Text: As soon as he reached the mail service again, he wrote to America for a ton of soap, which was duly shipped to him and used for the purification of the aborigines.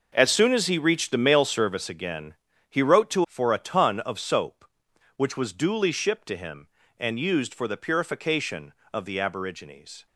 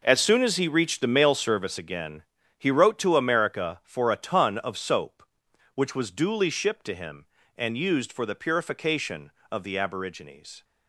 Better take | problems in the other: second | skips "America"; at 3.2 s

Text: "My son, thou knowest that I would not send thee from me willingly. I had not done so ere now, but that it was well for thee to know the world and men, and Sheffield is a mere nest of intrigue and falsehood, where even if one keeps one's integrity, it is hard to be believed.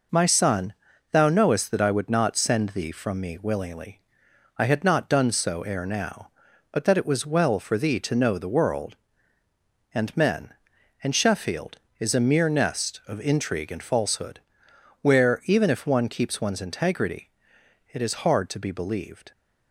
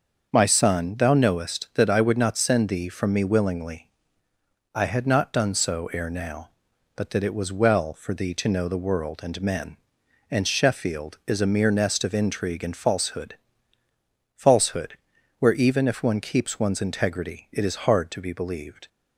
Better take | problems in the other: first | starts louder than the rest; until 1.3 s; 6.5 dB // says "falsehood" twice; at 14.3 s

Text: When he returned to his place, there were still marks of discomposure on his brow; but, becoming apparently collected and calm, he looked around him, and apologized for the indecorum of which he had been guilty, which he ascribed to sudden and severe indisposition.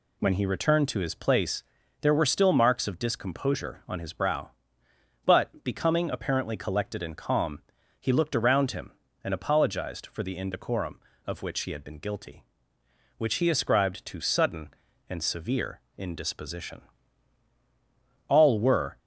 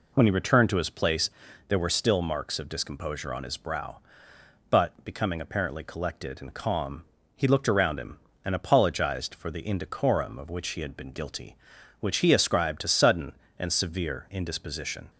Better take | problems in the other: second | pauses between "severe" and "indisposition"; slight; at 15.8 s; 0.16 s long // goes on to say "All were"; noticeable; from 18.2 s on; 0.72 s long

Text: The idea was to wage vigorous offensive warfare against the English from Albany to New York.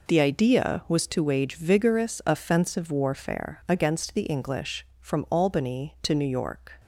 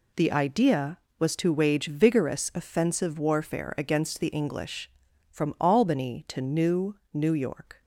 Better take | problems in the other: first | says "New" twice; at 7.1 s

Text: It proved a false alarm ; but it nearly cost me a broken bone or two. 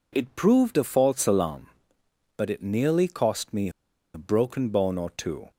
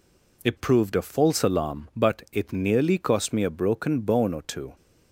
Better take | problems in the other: second | pauses between "a" and "broken"; at 3.7 s; 0.44 s long

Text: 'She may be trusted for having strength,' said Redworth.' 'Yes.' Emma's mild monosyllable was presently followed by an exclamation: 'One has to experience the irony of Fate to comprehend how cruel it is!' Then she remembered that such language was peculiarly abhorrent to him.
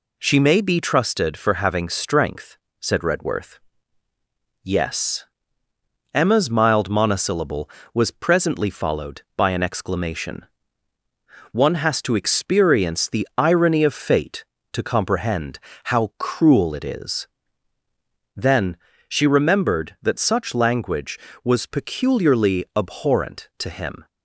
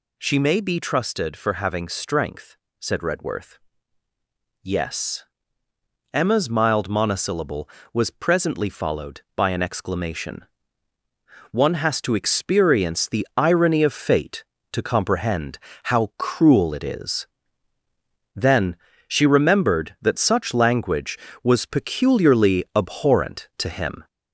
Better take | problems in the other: first | gets louder; throughout; 3.5 dB // pauses between "comprehend" and "how"; slight; at 15.5 s; 0.24 s long; slight in the first // pauses between "Then" and "she"; slight; at 18.7 s; 0.32 s long; slight in the first

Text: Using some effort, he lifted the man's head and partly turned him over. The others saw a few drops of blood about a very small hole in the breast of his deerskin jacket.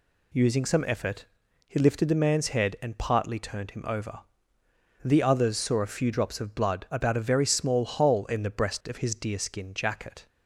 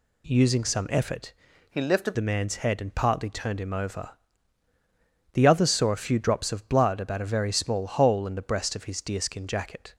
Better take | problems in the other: first | changes voice from "he" to "lifted"; from 1.6 to 2.1 s; 0.5 s long

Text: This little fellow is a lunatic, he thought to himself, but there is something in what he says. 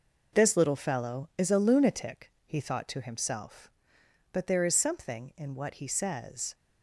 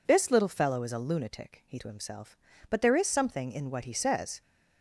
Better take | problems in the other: first | skips "thought"; at 1.7 s

